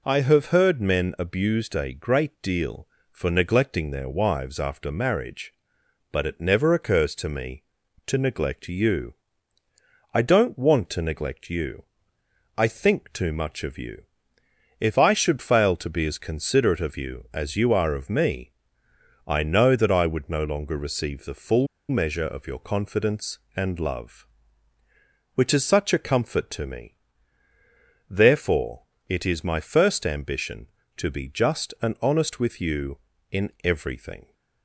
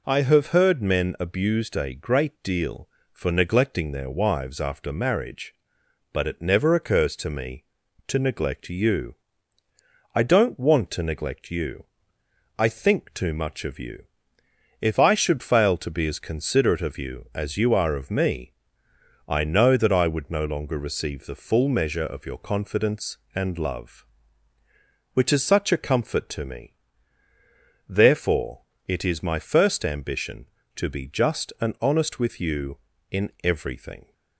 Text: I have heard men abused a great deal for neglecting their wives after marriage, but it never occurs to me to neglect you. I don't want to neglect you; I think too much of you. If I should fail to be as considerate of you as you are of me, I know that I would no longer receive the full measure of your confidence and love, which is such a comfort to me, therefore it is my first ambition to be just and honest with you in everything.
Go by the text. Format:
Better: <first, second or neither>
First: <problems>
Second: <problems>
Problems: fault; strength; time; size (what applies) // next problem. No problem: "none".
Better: second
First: pauses between "full" and "measure"; slight; at 21.6 s; 0.22 s long // pauses between "therefore" and "it"; slight; at 28.8 s; 0.26 s long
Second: pauses between "therefore" and "it"; slight; at 28.6 s; 0.26 s long